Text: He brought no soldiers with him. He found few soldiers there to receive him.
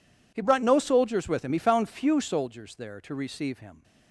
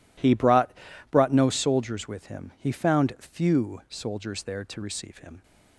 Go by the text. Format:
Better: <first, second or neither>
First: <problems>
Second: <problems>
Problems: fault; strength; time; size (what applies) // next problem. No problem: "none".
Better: first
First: none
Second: says "brought" twice; at 1.1 s